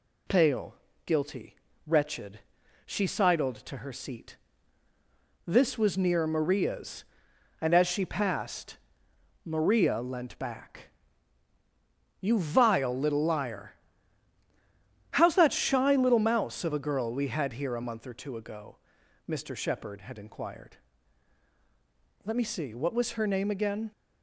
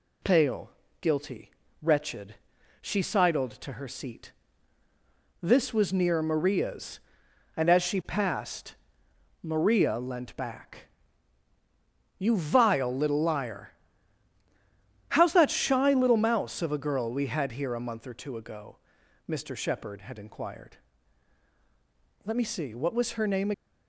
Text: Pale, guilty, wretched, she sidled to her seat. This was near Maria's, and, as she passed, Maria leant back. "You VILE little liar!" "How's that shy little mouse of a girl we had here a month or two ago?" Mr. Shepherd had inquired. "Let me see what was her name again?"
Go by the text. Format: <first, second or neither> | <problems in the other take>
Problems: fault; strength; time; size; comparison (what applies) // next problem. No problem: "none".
first | stops before "again"; at 23.5 s